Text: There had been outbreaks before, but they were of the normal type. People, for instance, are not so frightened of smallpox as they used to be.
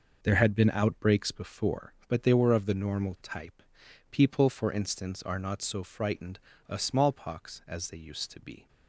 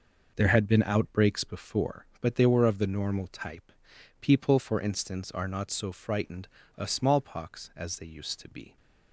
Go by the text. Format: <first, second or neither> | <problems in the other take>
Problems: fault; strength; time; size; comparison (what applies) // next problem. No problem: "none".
neither | none